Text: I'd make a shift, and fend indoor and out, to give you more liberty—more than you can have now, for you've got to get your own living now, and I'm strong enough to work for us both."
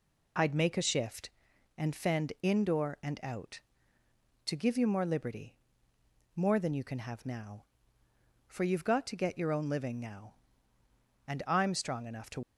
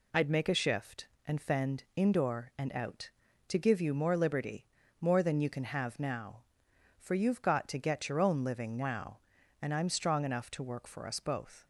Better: second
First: stops before "work for us both"; at 12.4 s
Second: none

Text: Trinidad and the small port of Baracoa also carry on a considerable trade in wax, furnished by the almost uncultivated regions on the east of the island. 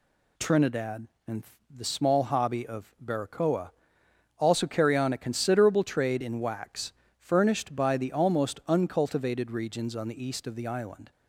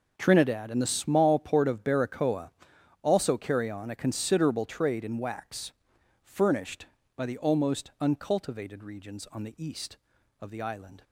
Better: second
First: pauses between "and" and "the"; slight; at 1.4 s; 0.30 s long // says "hobby" for "port"; at 2.2 s // pauses between "Baracoa" and "also"; noticeable; at 3.6 s; 0.68 s long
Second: pauses between "Baracoa" and "also"; noticeable; at 2.5 s; 0.52 s long

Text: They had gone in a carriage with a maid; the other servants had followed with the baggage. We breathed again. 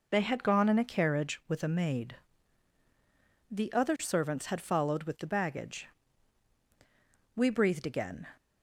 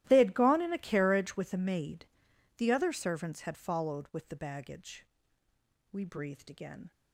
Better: first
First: none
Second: gets quieter; strong; throughout; 19 dB

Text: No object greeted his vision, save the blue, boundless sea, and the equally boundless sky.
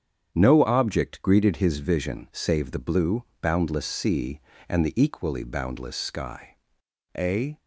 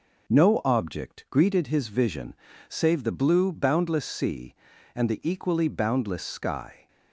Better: second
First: starts louder than the rest; strong; until 1.3 s; 8 dB // goes on to say "A"; slight; from 7.1 s on; 0.42 s long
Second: none

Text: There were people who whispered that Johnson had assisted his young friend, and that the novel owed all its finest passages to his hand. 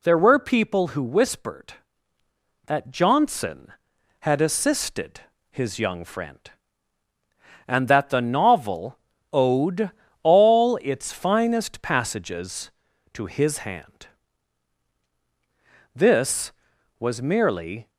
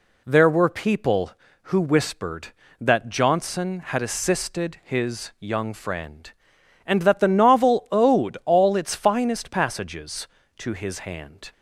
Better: second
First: pauses between "assisted" and "his"; slight; at 5.2 s; 0.28 s long // pauses between "novel" and "owed"; slight; at 8.9 s; 0.34 s long // pauses between "owed" and "all"; slight; at 9.9 s; 0.30 s long // goes on to say "This was merely"; strong; from 15.9 s on; 1.9 s long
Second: none

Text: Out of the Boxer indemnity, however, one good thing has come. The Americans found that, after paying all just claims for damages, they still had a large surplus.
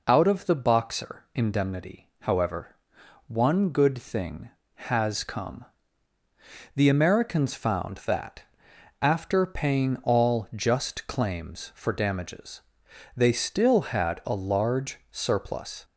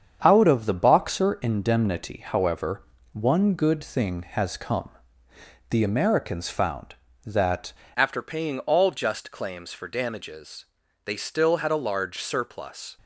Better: first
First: none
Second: starts louder than the rest; strong; until 1.2 s; 7.5 dB // changes voice at "after"; from 7.9 s on; 5.0 s long

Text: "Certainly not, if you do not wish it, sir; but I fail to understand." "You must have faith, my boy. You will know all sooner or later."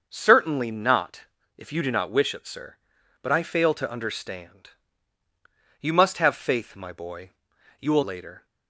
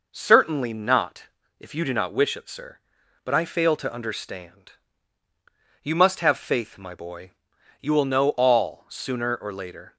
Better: second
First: starts louder than the rest; noticeable; until 1.0 s; 6 dB // skips "know all sooner or"; at 8.0 s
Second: none

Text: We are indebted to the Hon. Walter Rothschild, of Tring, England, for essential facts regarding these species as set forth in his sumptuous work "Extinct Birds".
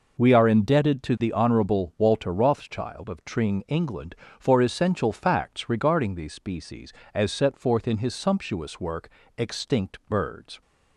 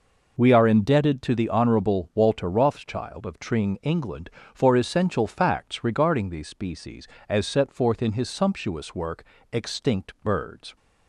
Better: neither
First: pauses between "work" and "Extinct"; slight; at 9.0 s; 0.30 s long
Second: pauses between "work" and "Extinct"; slight; at 9.2 s; 0.30 s long

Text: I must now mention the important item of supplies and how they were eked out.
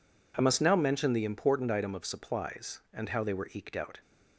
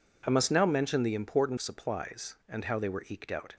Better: first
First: none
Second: skips "item of"; at 1.5 s

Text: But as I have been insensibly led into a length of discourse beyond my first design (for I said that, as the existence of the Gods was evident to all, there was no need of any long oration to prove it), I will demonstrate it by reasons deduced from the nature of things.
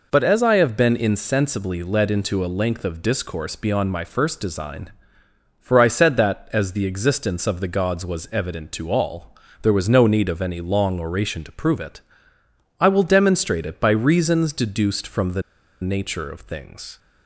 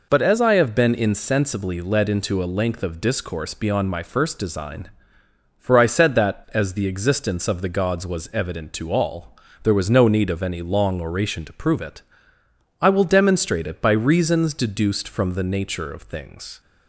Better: second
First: pauses between "the" and "nature"; at 15.4 s; 0.40 s long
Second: none

